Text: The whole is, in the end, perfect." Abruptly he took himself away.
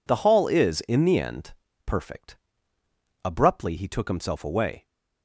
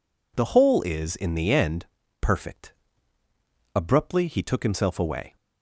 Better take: second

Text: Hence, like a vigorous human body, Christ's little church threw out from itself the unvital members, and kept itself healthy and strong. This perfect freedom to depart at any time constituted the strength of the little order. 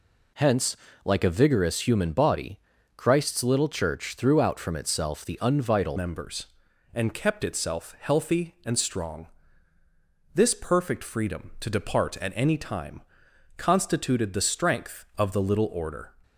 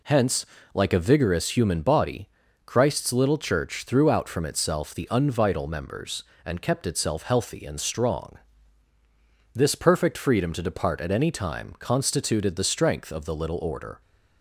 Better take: second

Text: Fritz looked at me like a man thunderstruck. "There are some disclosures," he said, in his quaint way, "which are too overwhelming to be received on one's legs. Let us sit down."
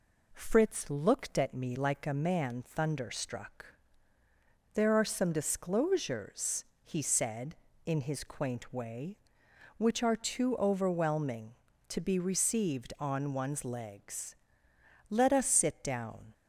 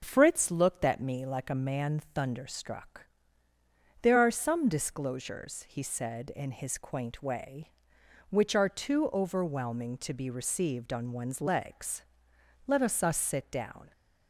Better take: first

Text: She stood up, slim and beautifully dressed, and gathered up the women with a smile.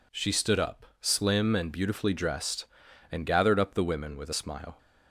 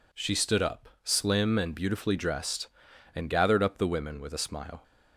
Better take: neither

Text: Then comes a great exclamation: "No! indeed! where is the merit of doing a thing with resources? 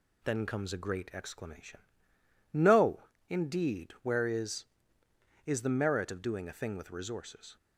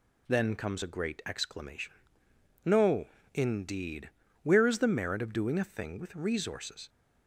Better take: second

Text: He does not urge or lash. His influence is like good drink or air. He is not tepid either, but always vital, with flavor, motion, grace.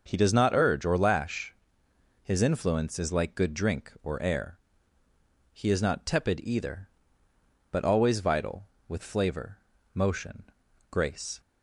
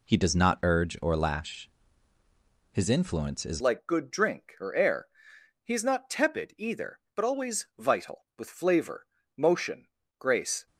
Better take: first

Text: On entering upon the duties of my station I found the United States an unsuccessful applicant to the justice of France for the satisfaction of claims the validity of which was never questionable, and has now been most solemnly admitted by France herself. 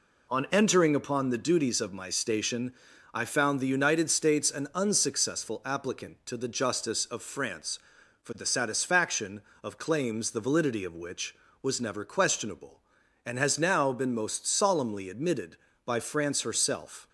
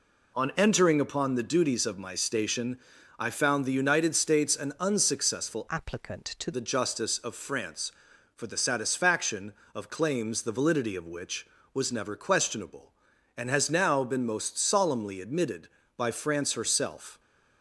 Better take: first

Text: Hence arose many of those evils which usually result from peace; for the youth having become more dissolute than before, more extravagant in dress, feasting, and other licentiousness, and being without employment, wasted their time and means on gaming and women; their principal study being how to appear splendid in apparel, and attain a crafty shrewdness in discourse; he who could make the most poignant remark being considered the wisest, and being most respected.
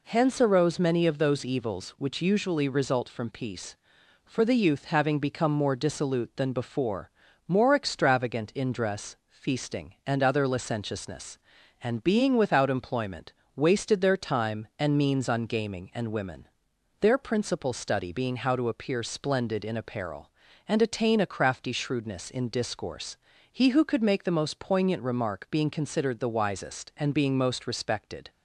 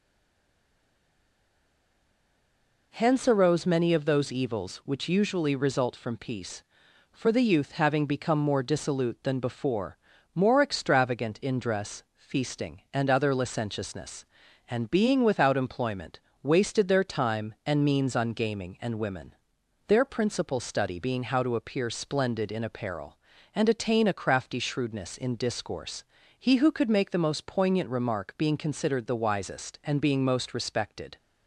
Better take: first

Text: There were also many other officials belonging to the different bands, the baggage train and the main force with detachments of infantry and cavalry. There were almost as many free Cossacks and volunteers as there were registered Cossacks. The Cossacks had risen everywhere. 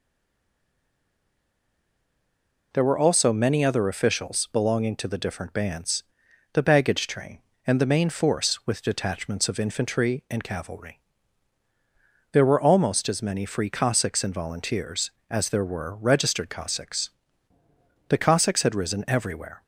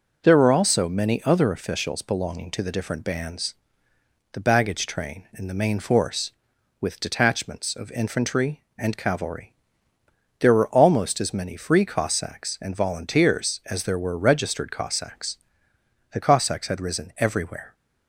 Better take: second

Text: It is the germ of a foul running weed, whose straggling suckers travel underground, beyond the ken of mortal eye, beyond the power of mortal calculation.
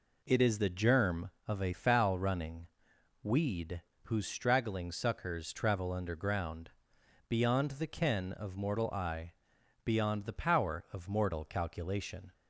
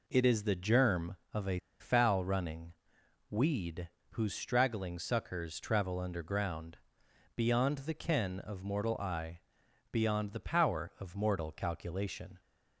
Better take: first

